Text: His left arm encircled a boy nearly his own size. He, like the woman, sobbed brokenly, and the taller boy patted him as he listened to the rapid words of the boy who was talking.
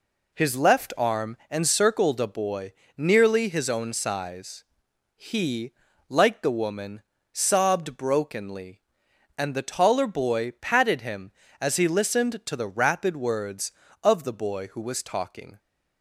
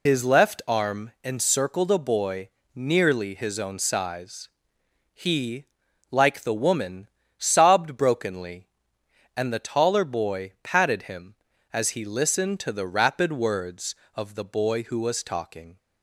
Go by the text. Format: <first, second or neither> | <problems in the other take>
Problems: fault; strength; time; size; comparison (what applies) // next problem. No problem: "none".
first | loses the start of "His"; at 0.0 s; 80 ms // pauses between "boy" and "nearly"; slight; at 2.4 s; 0.26 s long; slight in the first